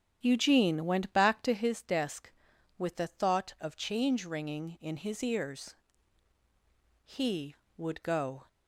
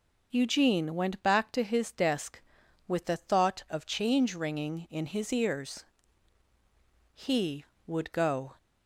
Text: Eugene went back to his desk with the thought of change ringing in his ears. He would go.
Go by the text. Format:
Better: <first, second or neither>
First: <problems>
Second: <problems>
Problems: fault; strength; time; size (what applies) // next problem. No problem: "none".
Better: second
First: starts louder than the rest; strong; until 1.8 s; 9 dB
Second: none